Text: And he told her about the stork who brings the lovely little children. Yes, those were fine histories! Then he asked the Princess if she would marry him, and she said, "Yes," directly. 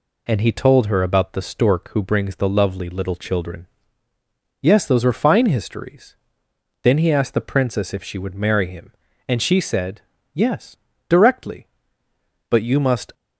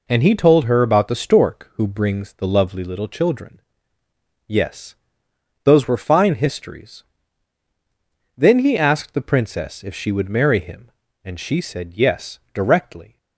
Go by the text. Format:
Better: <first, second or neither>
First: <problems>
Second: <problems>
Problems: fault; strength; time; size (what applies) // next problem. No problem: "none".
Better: second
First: goes on to say "But you must"; noticeable; from 12.4 s on; 0.64 s long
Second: none